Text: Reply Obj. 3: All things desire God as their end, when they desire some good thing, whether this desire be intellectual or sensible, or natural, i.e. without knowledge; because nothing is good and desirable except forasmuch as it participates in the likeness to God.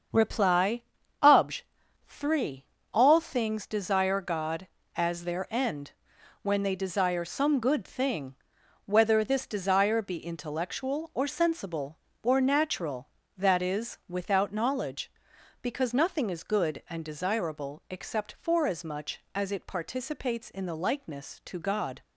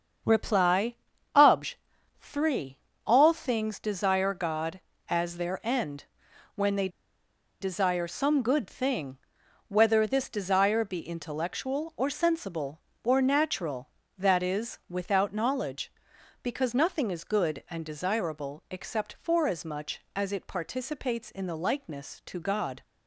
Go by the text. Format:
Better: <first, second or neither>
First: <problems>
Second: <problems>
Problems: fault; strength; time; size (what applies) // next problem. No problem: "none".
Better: first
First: starts louder than the rest; strong; until 1.5 s; 7 dB // pauses between "Reply" and "Obj"; at 0.8 s; 0.38 s long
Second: starts louder than the rest; strong; until 1.6 s; 7 dB // pauses between "Reply" and "Obj"; at 0.9 s; 0.38 s long // pauses between "they" and "desire"; noticeable; at 6.8 s; 0.72 s long